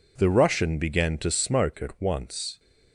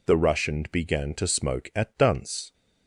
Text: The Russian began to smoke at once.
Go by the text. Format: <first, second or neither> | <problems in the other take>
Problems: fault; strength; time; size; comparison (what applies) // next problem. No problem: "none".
first | says "dunce" for "once"; at 1.9 s